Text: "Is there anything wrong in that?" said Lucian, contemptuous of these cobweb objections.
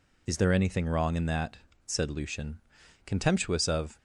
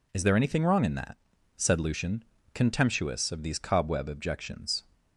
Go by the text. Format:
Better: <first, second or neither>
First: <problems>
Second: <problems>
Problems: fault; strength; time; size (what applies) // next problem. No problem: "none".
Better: second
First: stops before "these cobweb objections"; at 3.9 s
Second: none